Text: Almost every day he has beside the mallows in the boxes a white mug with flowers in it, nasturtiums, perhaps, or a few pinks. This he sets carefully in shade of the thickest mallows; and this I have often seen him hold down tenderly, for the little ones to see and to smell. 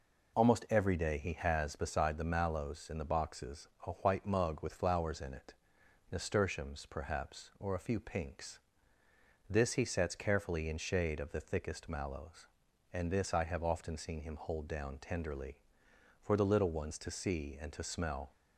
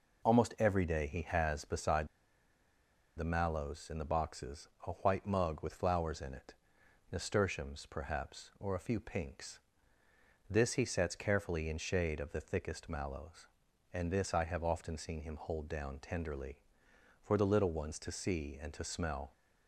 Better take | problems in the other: first | pauses between "beside" and "the"; at 2.0 s; 1.1 s long // pauses between "boxes" and "a"; slight; at 4.6 s; 0.18 s long; slight in the first

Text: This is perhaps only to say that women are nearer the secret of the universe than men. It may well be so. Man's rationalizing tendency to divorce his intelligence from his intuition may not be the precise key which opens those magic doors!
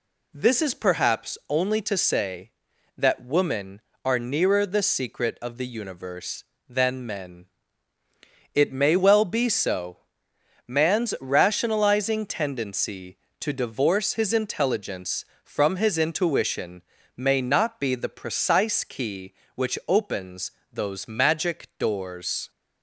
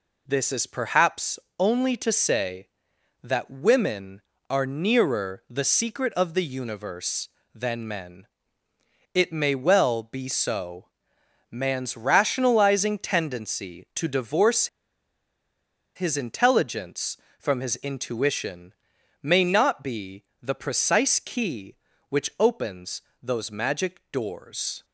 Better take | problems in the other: first | pauses between "perhaps" and "only"; slight; at 1.3 s; 0.18 s long // pauses between "divorce" and "his"; strong; at 14.6 s; 1.2 s long // pauses between "intuition" and "may"; noticeable; at 18.7 s; 0.50 s long; slight in the first // pauses between "be" and "the"; slight; at 20.2 s; 0.18 s long // pauses between "opens" and "those"; slight; at 23.0 s; 0.20 s long; slight in the first

